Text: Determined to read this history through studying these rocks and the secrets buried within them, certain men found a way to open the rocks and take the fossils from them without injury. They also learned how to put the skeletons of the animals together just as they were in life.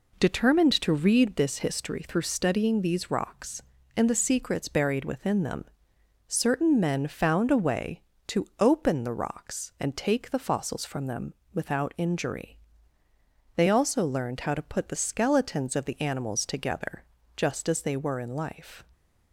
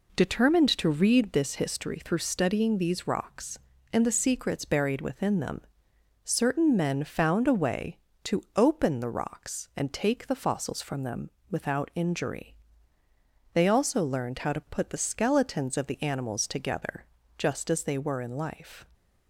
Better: neither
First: pauses between "them" and "without"; slight; at 11.3 s; 0.18 s long // pauses between "together" and "just"; slight; at 17.0 s; 0.30 s long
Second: pauses between "them" and "without"; slight; at 11.3 s; 0.18 s long // pauses between "together" and "just"; slight; at 17.0 s; 0.30 s long

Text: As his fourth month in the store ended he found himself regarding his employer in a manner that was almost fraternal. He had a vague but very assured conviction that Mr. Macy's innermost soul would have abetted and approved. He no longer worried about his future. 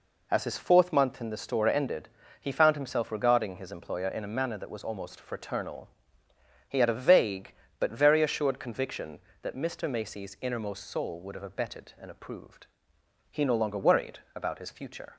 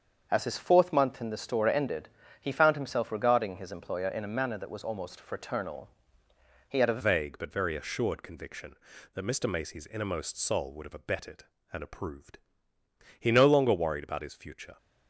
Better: first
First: pauses between "ended" and "he"; slight; at 2.0 s; 0.32 s long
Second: starts louder than the rest; until 1.3 s; 7 dB // pauses between "ended" and "he"; slight; at 2.0 s; 0.32 s long // changes voice at "vague"; from 7.0 s on; 7.7 s long

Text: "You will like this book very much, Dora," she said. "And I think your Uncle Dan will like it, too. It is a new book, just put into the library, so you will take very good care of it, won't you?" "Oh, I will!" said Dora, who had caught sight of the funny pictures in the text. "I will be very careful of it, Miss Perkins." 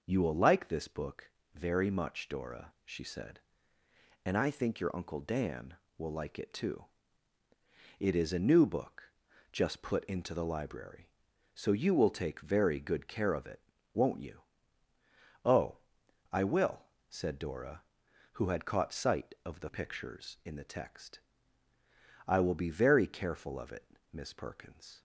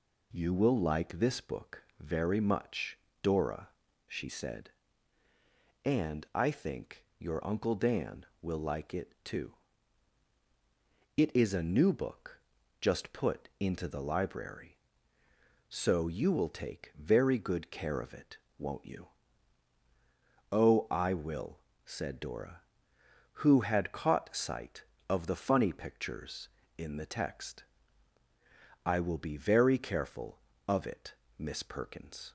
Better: second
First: pauses between "book" and "very"; slight; at 1.2 s; 0.24 s long // skips "funny"; at 19.6 s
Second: pauses between "book" and "very"; slight; at 1.8 s; 0.16 s long

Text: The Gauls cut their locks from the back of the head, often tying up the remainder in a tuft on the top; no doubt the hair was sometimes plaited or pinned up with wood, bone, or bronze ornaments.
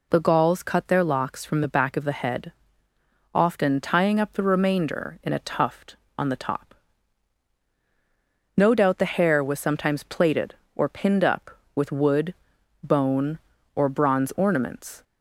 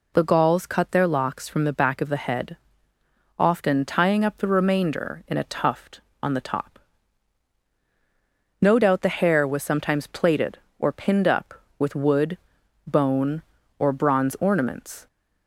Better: neither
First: none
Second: none

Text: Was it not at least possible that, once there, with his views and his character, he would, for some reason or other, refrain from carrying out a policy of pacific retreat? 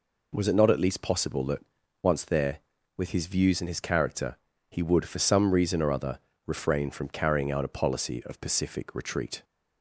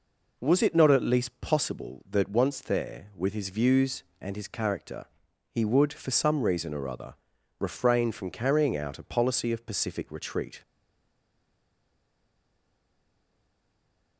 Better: first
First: none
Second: stays silent after the last word; strong; from 10.6 s on; 3.5 s long

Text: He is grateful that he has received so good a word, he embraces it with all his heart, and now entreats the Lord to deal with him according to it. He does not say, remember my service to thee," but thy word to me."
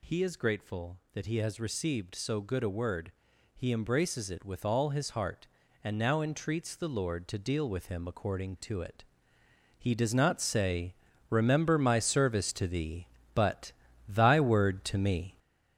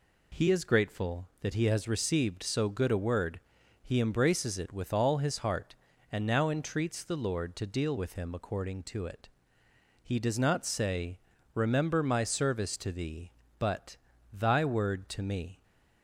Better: second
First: gets louder; noticeable; throughout; 5 dB // pauses between "but" and "thy"; slight; at 13.7 s; 0.36 s long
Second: pauses between "but" and "thy"; slight; at 13.9 s; 0.36 s long

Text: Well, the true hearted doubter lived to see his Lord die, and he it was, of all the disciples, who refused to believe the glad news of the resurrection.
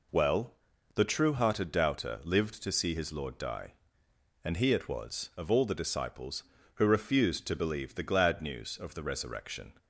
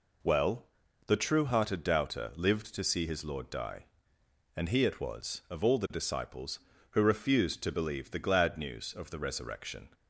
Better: neither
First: none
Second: none

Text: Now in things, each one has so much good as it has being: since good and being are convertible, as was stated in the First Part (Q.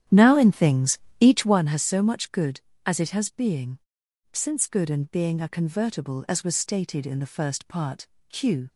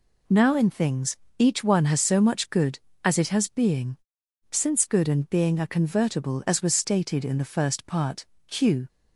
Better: second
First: starts louder than the rest; strong; until 1.6 s; 10 dB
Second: none

